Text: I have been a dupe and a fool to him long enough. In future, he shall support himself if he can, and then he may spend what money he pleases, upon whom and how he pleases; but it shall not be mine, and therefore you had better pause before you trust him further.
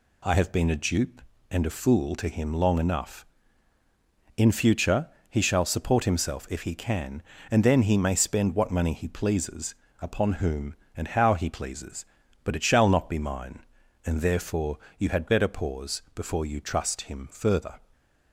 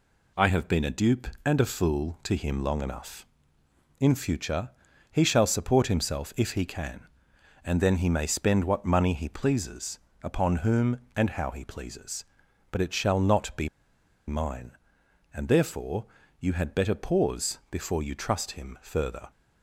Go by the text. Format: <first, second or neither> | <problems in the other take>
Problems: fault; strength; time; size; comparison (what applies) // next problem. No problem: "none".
first | pauses between "be" and "mine"; noticeable; at 13.6 s; 0.59 s long // pauses between "therefore" and "you"; slight; at 16.0 s; 0.36 s long; slight in the first